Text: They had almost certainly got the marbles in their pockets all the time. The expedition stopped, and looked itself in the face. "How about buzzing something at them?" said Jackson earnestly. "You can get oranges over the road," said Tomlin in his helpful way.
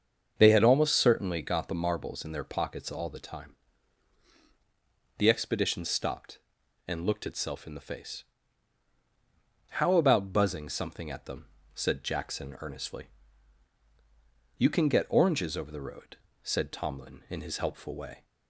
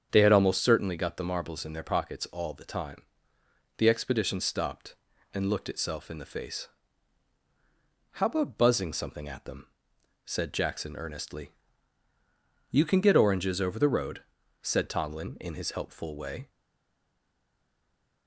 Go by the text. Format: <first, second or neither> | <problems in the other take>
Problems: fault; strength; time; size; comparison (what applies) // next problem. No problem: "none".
first | starts louder than the rest; strong; until 1.1 s; 8 dB; also in the first // stays silent after the last word; noticeable; from 16.4 s on; 1.8 s long